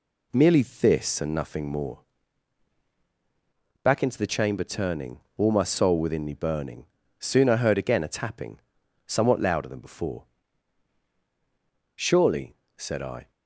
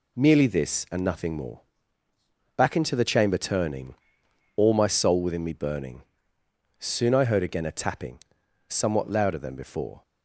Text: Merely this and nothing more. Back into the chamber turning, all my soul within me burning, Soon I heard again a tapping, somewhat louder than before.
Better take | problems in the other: second | goes on to say "Surely said I"; from 11.9 s on; 1.3 s long

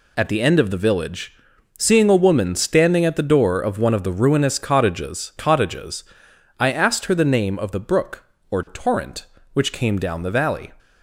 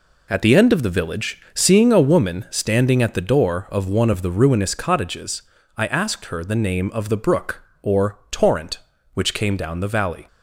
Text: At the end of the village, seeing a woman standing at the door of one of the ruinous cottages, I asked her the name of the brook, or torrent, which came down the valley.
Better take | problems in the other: second | says "cottages" twice; at 5.3 s

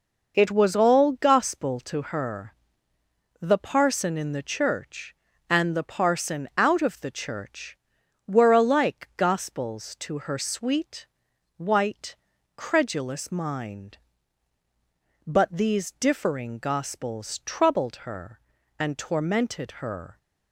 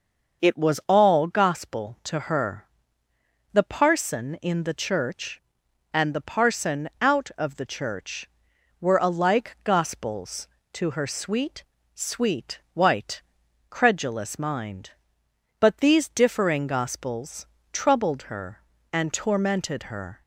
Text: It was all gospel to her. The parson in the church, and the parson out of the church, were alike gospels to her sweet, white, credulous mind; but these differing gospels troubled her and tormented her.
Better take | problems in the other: first | starts louder than the rest; noticeable; until 1.5 s; 6 dB // says "sweet" twice; at 11.9 s // pauses between "gospels" and "troubled"; slight; at 17.4 s; 0.28 s long

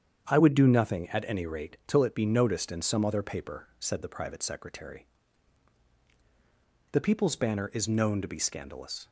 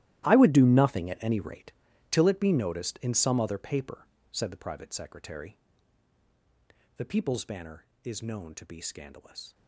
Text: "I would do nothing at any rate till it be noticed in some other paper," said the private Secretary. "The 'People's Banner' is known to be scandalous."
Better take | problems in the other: first | gets quieter; strong; throughout; 16.5 dB // starts louder than the rest; strong; until 1.2 s; 14 dB; strong in the first // pauses between "rate" and "till"; at 1.7 s; 0.40 s long

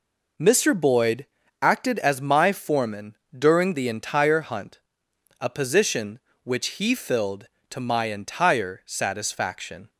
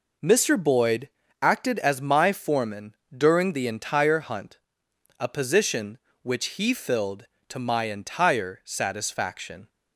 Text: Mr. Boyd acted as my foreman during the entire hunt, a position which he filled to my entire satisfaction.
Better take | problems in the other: neither | pauses between "Boyd" and "acted"; slight; the same in both // pauses between "foreman" and "during"; slight; the same in both

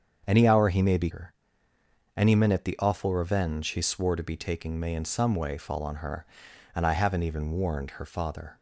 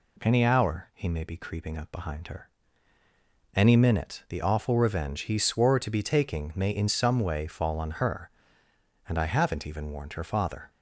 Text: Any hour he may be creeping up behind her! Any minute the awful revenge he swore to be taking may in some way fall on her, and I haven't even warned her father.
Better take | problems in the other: second | starts louder than the rest; until 1.2 s; 7 dB // skips "creeping up behind"; at 1.1 s

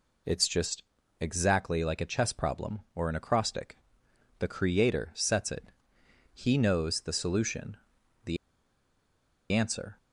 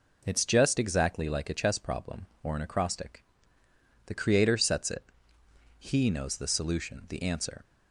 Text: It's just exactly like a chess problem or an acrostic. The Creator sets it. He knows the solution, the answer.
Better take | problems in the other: second | pauses between "just" and "exactly"; slight; at 0.8 s; 0.36 s long // pauses between "the" and "answer"; at 8.3 s; 1.1 s long

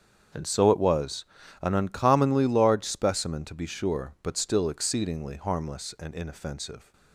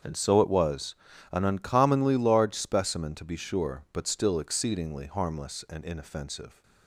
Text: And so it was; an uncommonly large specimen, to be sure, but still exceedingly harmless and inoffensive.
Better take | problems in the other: neither | starts louder than the rest; strong; the same in both

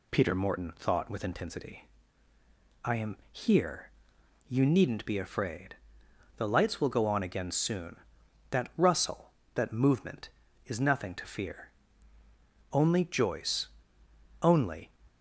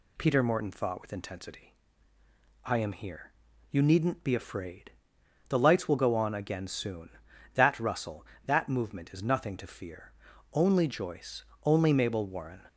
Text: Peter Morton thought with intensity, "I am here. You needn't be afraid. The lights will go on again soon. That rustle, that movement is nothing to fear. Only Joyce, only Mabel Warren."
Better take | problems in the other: second | stops before "Mabel Warren"; at 15.0 s

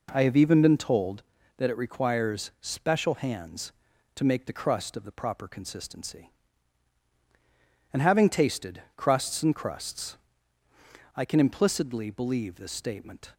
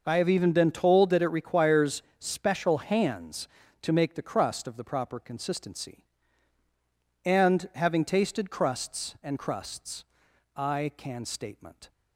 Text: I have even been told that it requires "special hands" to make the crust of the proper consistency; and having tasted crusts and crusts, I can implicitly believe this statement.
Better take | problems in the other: first | pauses between "requires" and "special"; slight; at 2.0 s; 0.16 s long // skips "implicitly believe this"; at 11.2 s

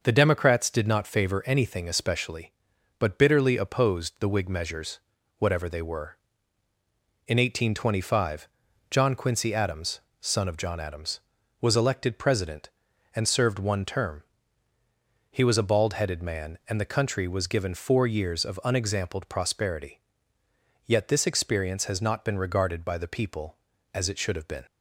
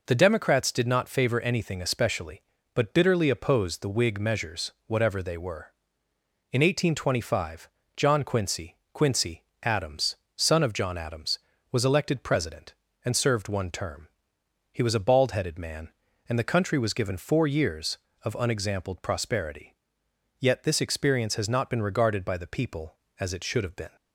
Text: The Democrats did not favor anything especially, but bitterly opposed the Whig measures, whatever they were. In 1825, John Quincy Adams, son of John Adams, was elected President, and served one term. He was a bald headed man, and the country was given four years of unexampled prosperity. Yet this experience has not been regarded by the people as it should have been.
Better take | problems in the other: first | says "Quincy" twice; at 8.9 s

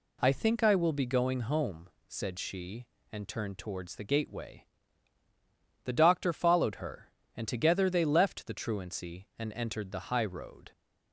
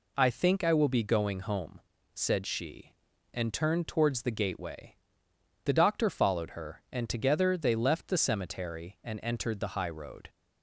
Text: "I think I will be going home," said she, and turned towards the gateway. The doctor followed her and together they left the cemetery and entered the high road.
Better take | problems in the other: second | says "truancy" for "cemetery"; at 8.5 s

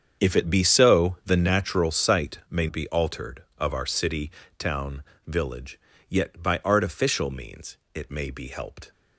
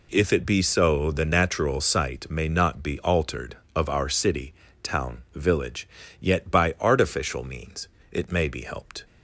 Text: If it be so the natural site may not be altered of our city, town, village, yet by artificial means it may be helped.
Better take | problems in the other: second | starts louder than the rest; strong; until 1.2 s; 7.5 dB // skips "not"; at 2.6 s // pauses between "means" and "it"; slight; at 7.7 s; 0.18 s long; slight in the second

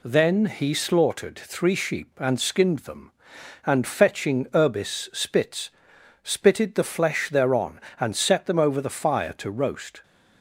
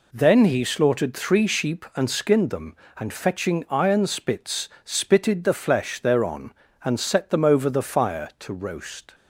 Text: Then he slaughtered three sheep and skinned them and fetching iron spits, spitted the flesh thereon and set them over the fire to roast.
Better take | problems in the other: second | says "urbis" for "iron"; at 4.5 s

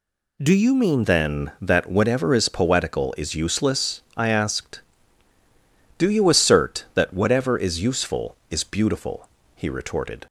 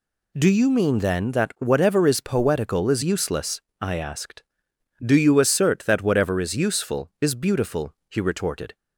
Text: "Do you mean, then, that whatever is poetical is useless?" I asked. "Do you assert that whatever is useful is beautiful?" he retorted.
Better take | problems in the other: second | changes voice at "then"; from 1.0 s on; 9.2 s long

